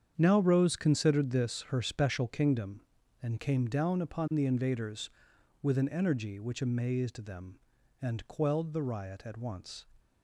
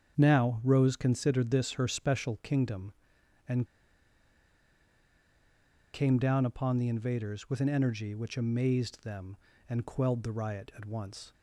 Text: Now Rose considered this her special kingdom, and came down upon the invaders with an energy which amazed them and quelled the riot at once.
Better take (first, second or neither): first